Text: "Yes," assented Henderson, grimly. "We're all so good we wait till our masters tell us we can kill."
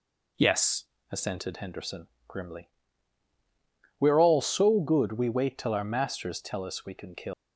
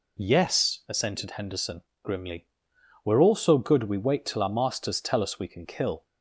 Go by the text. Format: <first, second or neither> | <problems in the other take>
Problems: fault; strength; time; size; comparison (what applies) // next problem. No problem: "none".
second | leaves "kill" unfinished; at 7.3 s; 135 ms